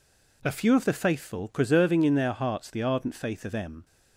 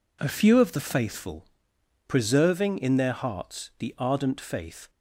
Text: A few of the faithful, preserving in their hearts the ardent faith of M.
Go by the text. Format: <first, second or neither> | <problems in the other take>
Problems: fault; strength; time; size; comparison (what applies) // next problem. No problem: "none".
first | stops before "of M"; at 4.8 s